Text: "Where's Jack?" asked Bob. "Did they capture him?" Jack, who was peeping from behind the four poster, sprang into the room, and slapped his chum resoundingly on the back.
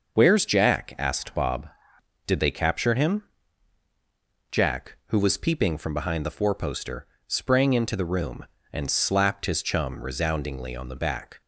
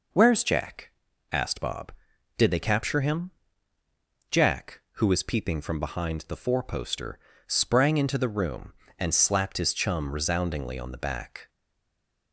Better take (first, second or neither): first